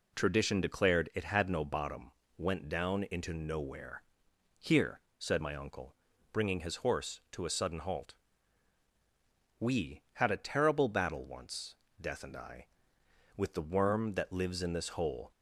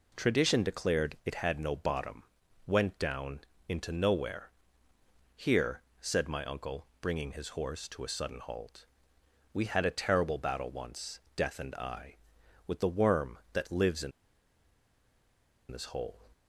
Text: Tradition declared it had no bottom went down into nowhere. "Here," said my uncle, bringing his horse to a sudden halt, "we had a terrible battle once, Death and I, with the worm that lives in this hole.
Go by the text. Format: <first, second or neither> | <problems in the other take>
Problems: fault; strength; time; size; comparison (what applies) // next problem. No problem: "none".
first | pauses between "bottom" and "went"; at 2.2 s; 0.42 s long; slight in the first // pauses between "down" and "into"; slight; at 3.4 s; 0.28 s long // pauses between "in" and "this"; strong; at 14.1 s; 1.6 s long